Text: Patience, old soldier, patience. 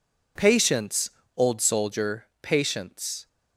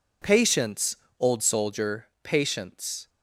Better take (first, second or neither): neither